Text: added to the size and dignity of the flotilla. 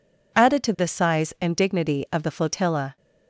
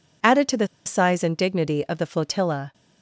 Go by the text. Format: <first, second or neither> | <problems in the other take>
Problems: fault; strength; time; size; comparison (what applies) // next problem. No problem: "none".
first | pauses between "the" and "size"; slight; at 0.6 s; 0.19 s long